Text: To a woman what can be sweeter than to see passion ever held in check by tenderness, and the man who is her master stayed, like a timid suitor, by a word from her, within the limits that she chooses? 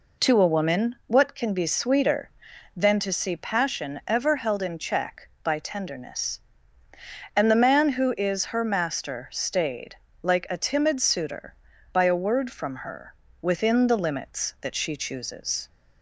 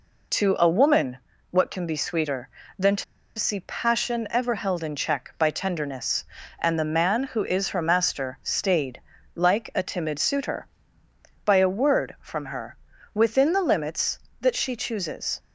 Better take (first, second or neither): first